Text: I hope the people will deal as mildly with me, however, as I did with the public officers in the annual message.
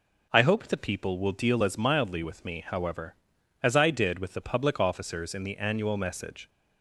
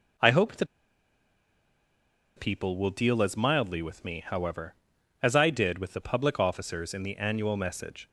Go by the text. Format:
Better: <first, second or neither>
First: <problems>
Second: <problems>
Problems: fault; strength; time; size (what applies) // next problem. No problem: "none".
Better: first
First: none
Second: pauses between "the" and "people"; strong; at 0.6 s; 1.7 s long